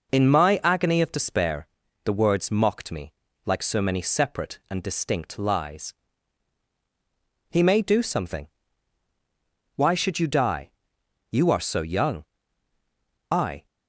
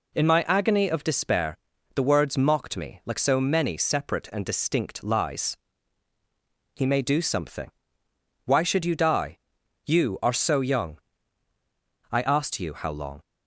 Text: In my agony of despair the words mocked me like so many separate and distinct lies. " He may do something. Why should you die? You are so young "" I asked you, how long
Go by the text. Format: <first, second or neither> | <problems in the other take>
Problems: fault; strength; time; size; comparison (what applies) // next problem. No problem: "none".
second | pauses between "despair" and "the"; slight; at 1.6 s; 0.36 s long; also in the second // pauses between "me" and "like"; slight; at 3.1 s; 0.34 s long // stops before "asked you how long"; at 13.6 s